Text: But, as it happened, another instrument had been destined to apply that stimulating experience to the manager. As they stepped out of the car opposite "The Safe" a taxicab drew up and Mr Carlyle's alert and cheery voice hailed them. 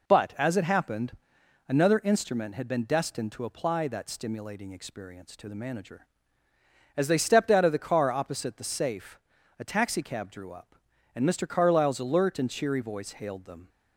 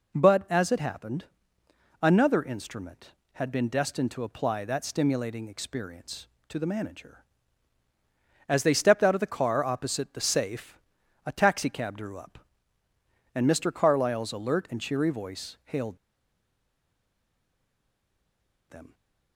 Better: first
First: pauses between "Safe" and "a"; at 9.1 s; 0.40 s long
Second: pauses between "Safe" and "a"; noticeable; at 10.7 s; 0.46 s long // pauses between "hailed" and "them"; strong; at 15.9 s; 2.7 s long

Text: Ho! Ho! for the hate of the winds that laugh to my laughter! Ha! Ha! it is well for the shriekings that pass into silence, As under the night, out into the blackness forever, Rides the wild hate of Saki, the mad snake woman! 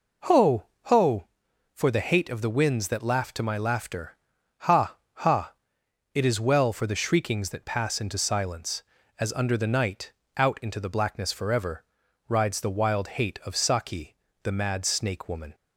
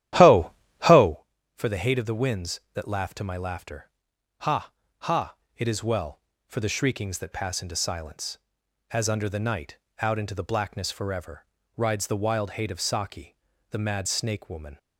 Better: first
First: none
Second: starts louder than the rest; strong; until 1.2 s; 12 dB

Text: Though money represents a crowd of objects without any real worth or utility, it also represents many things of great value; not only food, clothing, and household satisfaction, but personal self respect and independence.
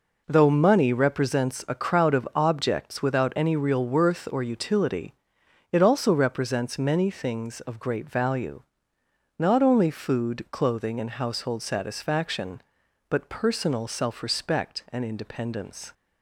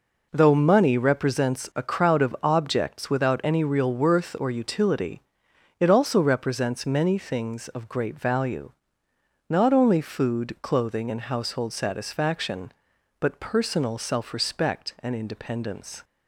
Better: neither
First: none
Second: none

